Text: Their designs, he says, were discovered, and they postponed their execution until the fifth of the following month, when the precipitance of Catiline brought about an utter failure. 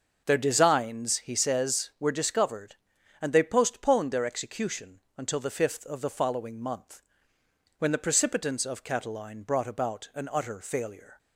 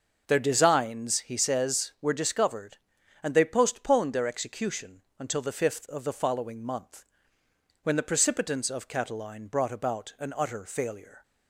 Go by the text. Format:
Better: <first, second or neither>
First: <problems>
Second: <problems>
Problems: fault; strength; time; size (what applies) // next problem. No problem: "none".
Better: neither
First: starts louder than the rest; noticeable; until 1.2 s; 6 dB // pauses between "execution" and "until"; slight; at 4.9 s; 0.18 s long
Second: starts louder than the rest; noticeable; until 1.2 s; 6 dB // pauses between "execution" and "until"; slight; at 5.0 s; 0.18 s long